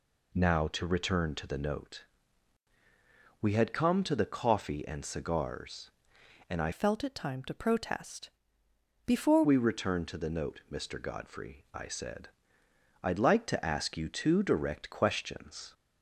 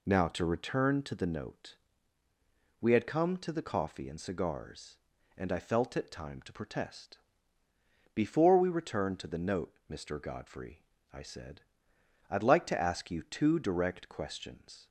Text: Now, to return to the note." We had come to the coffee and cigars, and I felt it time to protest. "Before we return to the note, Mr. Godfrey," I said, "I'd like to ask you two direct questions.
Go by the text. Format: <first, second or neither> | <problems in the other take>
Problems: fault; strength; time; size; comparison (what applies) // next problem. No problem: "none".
second | changes voice from "felt" to "Before"; from 6.7 to 9.4 s; 2.7 s long